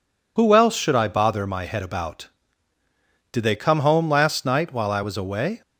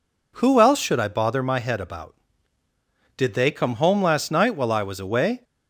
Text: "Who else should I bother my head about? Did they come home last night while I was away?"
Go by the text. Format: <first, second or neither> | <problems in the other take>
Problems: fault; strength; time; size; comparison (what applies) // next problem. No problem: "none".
second | loses the start of "Who"; at 0.3 s; 30 ms